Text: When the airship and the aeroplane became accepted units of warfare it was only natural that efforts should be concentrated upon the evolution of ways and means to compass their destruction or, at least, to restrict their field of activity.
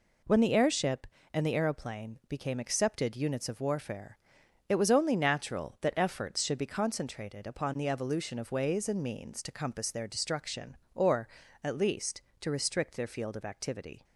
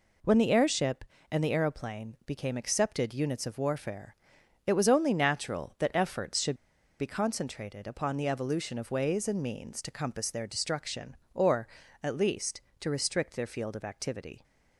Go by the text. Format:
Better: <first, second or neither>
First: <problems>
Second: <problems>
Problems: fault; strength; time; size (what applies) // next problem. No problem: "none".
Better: first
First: pauses between "warfare" and "it"; noticeable; at 4.1 s; 0.50 s long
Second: pauses between "warfare" and "it"; noticeable; at 4.1 s; 0.50 s long // pauses between "should" and "be"; at 6.5 s; 0.45 s long